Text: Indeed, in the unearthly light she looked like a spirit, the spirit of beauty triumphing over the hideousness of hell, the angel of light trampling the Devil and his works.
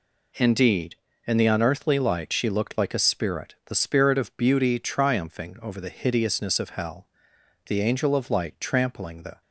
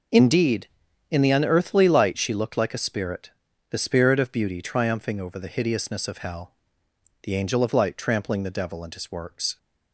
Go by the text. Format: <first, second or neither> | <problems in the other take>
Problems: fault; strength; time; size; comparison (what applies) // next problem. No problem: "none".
second | stops before "Devil and his works"; at 9.4 s